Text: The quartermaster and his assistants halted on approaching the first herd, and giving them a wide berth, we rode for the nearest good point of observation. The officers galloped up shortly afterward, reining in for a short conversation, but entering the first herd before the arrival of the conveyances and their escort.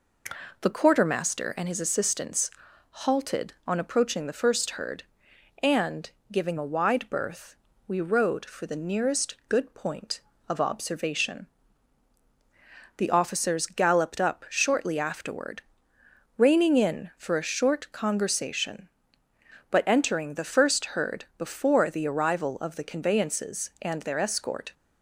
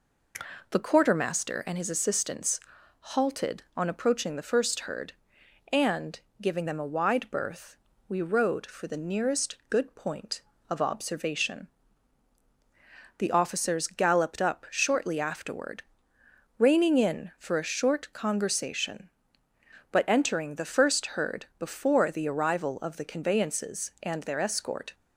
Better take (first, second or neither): second